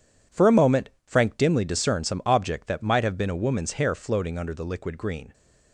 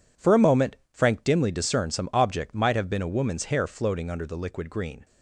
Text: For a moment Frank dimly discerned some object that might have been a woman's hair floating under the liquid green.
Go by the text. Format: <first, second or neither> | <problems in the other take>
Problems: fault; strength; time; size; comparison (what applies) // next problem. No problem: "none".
first | pauses between "moment" and "Frank"; slight; at 0.7 s; 0.16 s long; slight in the first // skips "that"; at 2.5 s